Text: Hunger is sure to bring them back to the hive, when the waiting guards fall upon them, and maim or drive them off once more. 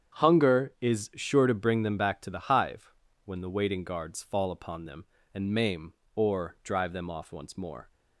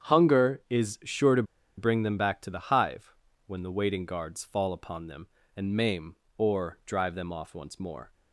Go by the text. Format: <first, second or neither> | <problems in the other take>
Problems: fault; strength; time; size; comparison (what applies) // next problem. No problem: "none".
first | starts louder than the rest; strong; until 1.1 s; 8 dB; strong in the first // pauses between "to" and "bring"; slight; at 1.4 s; 0.33 s long